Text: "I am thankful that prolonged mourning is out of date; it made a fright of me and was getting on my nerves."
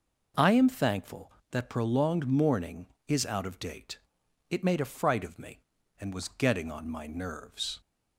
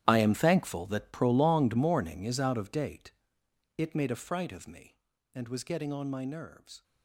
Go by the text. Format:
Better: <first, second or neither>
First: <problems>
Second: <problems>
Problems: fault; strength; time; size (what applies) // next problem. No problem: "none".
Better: first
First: none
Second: gets quieter; strong; throughout; 16.5 dB